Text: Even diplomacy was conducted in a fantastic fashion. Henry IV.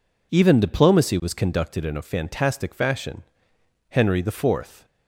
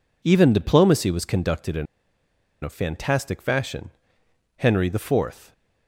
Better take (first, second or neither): first